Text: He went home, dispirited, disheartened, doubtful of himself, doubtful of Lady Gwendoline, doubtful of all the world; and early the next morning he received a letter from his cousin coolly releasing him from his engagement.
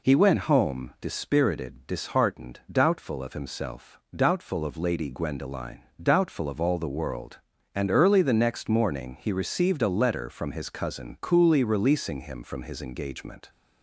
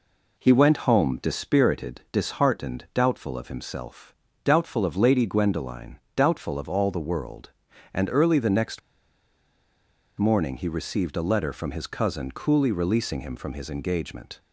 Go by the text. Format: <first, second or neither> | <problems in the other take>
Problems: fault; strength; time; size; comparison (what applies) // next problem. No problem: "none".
first | pauses between "next" and "morning"; strong; at 8.7 s; 1.3 s long